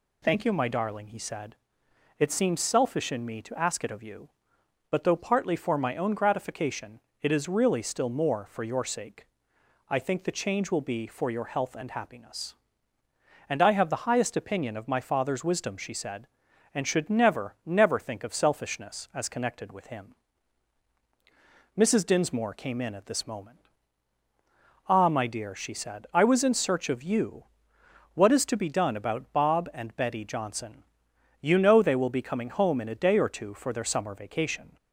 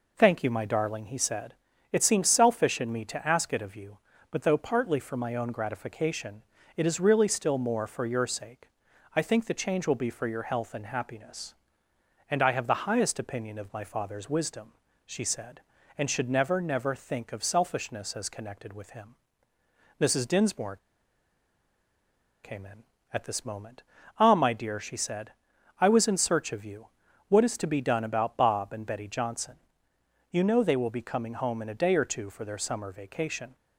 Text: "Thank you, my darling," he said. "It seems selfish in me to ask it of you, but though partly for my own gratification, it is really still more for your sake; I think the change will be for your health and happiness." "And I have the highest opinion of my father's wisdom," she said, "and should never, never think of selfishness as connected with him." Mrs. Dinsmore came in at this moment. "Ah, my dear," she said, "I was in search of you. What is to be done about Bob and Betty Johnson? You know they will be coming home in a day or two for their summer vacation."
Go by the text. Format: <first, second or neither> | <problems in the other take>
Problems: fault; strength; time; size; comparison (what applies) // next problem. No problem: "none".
first | pauses between "Dinsmore" and "came"; strong; at 20.7 s; 1.6 s long